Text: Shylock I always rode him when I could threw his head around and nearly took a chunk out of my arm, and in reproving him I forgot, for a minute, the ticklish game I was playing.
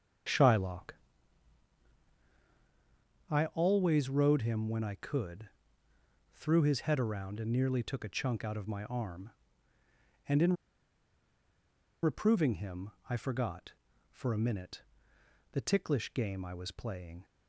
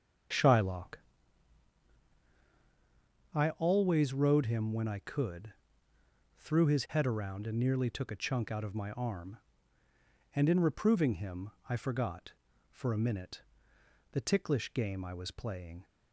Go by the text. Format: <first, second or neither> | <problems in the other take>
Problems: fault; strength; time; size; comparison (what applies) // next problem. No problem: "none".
second | starts louder than the rest; until 3.6 s; 7 dB; also in the second // pauses between "Shylock" and "I"; strong; at 0.9 s; 2.3 s long; strong in the second // pauses between "could" and "threw"; noticeable; at 5.4 s; 0.86 s long; noticeable in the second // pauses between "in" and "reproving"; strong; at 10.5 s; 1.4 s long // pauses between "him" and "I"; slight; at 12.9 s; 0.18 s long; slight in the second